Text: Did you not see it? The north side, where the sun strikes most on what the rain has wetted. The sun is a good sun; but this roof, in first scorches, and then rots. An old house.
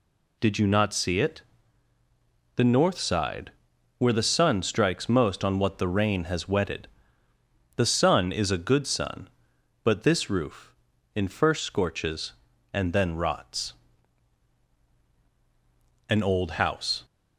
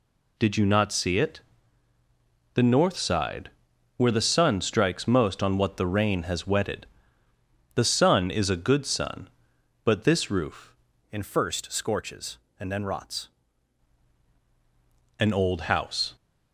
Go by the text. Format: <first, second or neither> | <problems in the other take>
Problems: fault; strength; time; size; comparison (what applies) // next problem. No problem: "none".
first | changes voice from "in" to "rots"; from 11.1 to 13.2 s; 2.1 s long